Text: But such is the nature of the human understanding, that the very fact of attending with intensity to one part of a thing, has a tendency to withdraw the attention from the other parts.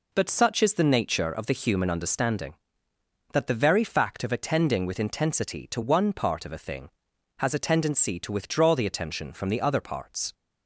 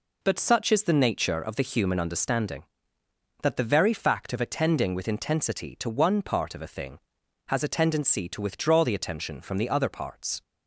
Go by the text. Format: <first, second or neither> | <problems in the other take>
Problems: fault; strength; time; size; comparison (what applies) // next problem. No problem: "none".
neither | none